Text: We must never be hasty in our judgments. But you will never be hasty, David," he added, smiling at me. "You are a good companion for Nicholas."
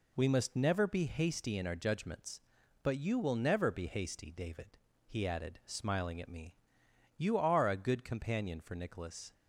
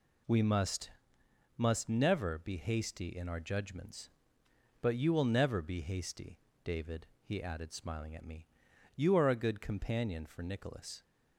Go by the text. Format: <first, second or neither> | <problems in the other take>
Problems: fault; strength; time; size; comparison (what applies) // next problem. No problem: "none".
first | says "must" twice; at 1.5 s